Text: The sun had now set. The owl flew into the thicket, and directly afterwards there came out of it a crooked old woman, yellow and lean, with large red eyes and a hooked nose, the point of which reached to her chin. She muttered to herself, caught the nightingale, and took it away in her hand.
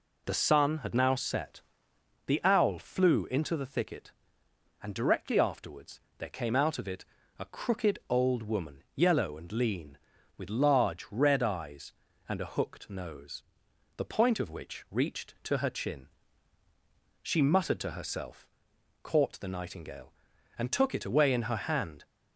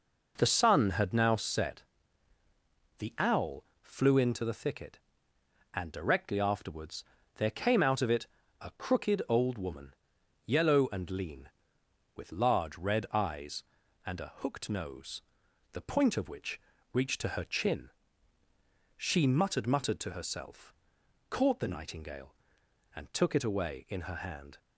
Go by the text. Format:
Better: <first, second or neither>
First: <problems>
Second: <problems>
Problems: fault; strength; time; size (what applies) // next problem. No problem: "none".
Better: first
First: pauses between "afterwards" and "there"; slight; at 6.0 s; 0.18 s long // pauses between "it" and "a"; slight; at 7.0 s; 0.34 s long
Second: pauses between "owl" and "flew"; slight; at 3.6 s; 0.18 s long // pauses between "afterwards" and "there"; slight; at 7.0 s; 0.32 s long // pauses between "it" and "a"; slight; at 8.2 s; 0.34 s long // pauses between "which" and "reached"; slight; at 16.6 s; 0.32 s long // says "muttered" twice; at 19.6 s